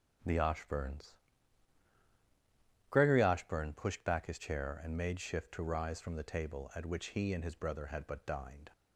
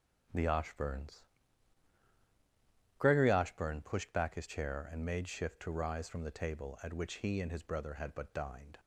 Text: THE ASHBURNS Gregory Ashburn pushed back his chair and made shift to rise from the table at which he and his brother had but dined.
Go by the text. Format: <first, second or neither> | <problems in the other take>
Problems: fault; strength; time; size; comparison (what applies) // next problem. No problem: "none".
neither | starts louder than the rest; the same in both // pauses between "ASHBURNS" and "Gregory"; strong; the same in both